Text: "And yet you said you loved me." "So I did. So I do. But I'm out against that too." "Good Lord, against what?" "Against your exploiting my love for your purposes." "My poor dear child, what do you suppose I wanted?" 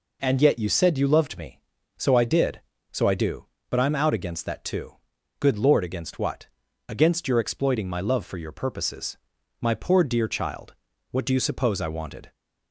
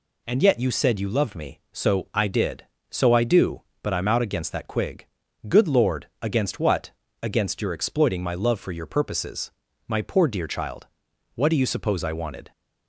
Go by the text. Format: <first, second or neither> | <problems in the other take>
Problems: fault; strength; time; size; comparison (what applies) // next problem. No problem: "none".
first | says "quig" for "too"; at 4.6 s